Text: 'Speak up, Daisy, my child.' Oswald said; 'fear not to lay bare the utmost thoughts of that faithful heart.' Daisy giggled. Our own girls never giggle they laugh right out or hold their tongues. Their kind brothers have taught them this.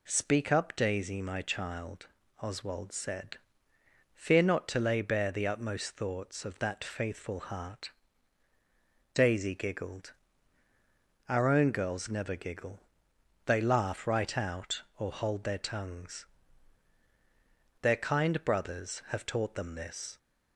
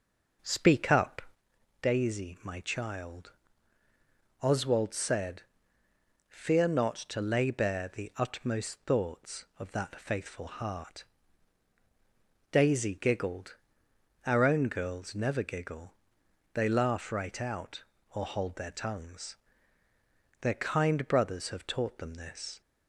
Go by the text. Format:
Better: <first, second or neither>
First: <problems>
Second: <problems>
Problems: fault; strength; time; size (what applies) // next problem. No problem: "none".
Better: first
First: pauses between "giggle" and "they"; noticeable; at 12.8 s; 0.64 s long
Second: starts louder than the rest; noticeable; until 1.4 s; 5.5 dB // pauses between "giggle" and "they"; noticeable; at 15.9 s; 0.62 s long